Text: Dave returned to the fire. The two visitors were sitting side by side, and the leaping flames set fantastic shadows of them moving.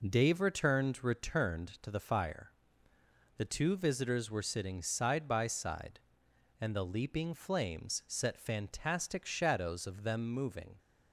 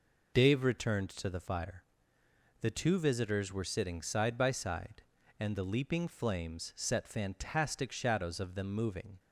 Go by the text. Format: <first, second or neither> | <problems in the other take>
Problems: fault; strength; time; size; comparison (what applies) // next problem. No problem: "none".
second | says "returned" twice; at 1.0 s